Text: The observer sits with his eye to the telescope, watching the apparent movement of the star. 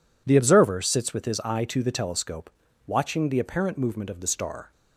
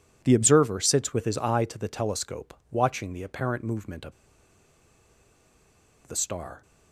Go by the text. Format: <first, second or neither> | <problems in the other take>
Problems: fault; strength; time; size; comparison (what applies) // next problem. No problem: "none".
first | pauses between "of" and "the"; strong; at 4.1 s; 1.9 s long